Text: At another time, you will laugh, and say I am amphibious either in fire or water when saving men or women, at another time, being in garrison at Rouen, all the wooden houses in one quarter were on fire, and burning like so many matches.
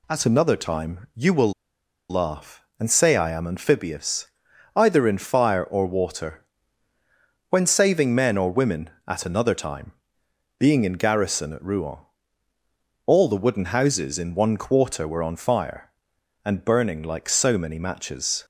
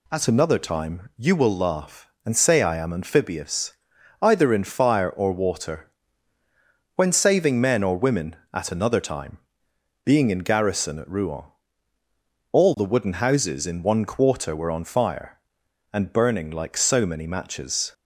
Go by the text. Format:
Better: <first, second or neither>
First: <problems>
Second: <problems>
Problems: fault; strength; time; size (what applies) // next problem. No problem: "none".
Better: second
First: pauses between "will" and "laugh"; noticeable; at 1.5 s; 0.57 s long // pauses between "amphibious" and "either"; noticeable; at 4.2 s; 0.46 s long // pauses between "water" and "when"; at 6.4 s; 1.0 s long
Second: pauses between "amphibious" and "either"; noticeable; at 3.7 s; 0.46 s long // pauses between "water" and "when"; at 5.9 s; 1.0 s long